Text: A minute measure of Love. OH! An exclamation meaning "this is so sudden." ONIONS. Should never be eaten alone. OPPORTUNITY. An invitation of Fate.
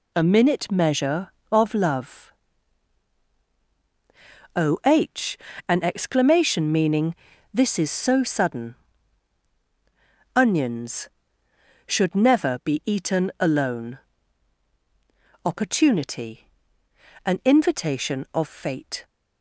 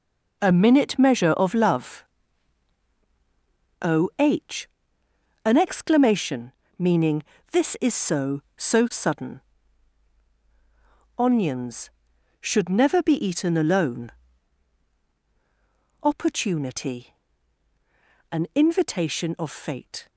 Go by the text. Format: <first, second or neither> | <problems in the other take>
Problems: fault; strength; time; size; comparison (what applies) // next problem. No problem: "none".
first | pauses between "exclamation" and "meaning"; slight; at 6.5 s; 0.24 s long // pauses between "meaning" and "this"; slight; at 7.2 s; 0.30 s long; also in the first // says "so" twice; at 8.5 s